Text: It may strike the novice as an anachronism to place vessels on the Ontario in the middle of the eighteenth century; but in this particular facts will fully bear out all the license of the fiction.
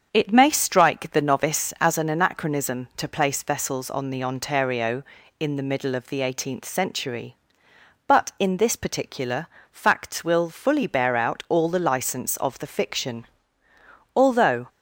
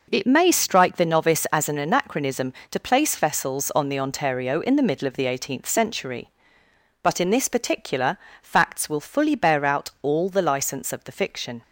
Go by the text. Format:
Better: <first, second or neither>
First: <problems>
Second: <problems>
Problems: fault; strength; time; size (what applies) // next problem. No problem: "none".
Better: second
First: starts louder than the rest; strong; until 1.1 s; 7.5 dB // pauses between "particular" and "facts"; slight; at 9.4 s; 0.26 s long // goes on to say "Although"; from 14.1 s on; 0.50 s long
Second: pauses between "particular" and "facts"; slight; at 8.1 s; 0.24 s long